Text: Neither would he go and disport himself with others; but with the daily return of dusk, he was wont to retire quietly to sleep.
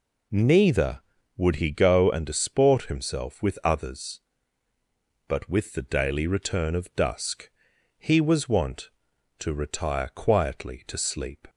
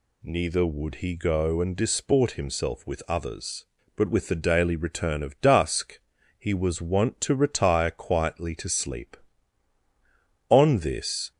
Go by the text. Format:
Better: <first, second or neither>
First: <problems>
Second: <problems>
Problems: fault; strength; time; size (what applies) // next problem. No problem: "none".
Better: first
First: none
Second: goes on to say "On this"; noticeable; from 10.4 s on; 0.82 s long